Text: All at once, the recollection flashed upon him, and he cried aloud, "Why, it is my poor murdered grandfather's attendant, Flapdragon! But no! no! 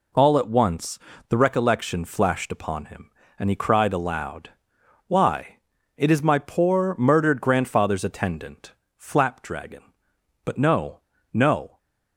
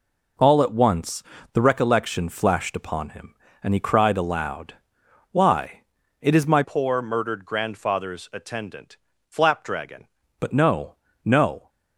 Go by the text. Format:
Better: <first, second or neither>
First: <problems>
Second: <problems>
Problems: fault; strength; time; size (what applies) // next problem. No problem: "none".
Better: first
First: none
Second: changes voice from "poor" to "Flapdragon"; from 6.6 to 10.0 s; 3.4 s long